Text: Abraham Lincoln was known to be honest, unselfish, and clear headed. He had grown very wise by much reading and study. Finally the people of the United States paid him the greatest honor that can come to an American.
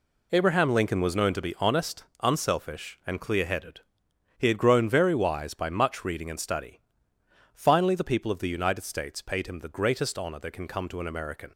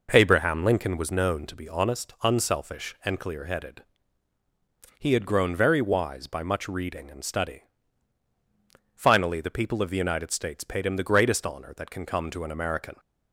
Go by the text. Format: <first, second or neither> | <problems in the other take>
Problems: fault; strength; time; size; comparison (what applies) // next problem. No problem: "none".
first | starts louder than the rest; noticeable; until 1.5 s; 5 dB